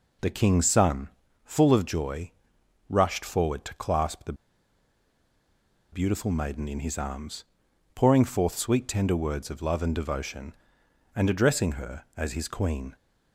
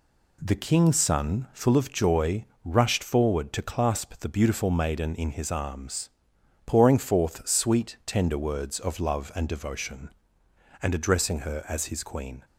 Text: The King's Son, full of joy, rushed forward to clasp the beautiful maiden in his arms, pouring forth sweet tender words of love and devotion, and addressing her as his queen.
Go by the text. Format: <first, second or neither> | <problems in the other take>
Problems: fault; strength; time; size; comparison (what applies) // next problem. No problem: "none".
second | pauses between "the" and "beautiful"; strong; at 4.3 s; 1.5 s long